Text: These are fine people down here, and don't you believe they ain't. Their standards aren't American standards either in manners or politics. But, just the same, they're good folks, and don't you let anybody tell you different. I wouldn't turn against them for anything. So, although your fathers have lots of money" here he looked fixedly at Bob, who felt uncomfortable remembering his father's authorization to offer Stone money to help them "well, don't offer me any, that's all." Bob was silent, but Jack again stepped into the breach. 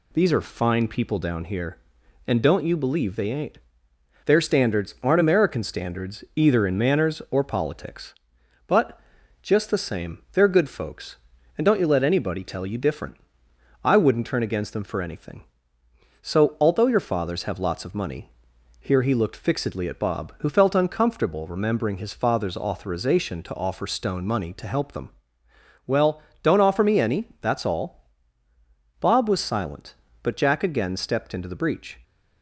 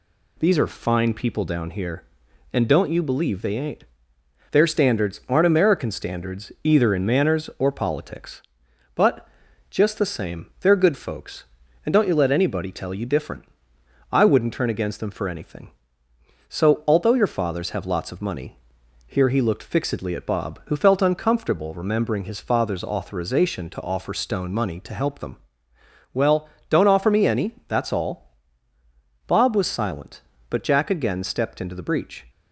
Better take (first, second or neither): neither